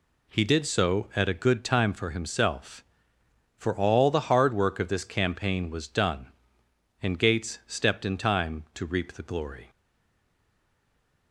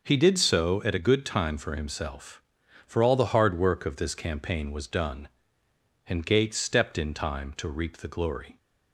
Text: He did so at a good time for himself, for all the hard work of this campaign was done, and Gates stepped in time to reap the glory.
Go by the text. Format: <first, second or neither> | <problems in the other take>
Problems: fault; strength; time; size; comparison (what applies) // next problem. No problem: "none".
second | stays silent after the last word; noticeable; from 9.6 s on; 1.7 s long